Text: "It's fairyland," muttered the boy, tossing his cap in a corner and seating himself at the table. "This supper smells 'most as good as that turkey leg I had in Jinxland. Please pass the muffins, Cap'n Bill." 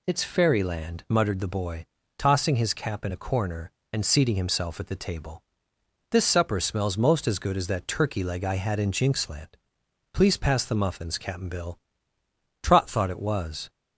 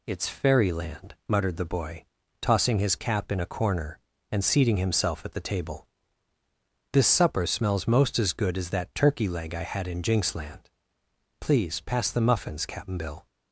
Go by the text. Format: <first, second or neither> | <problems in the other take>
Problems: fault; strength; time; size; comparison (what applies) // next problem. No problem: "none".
second | goes on to say "Trot thought it was"; noticeable; from 12.6 s on; 1.0 s long